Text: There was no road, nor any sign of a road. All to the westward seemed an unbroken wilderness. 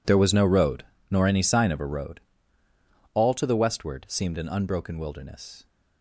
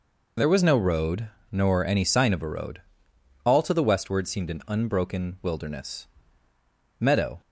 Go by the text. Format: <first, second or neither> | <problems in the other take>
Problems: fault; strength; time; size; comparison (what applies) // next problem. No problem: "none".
first | goes on to say "Meadow"; slight; from 7.0 s on; 0.40 s long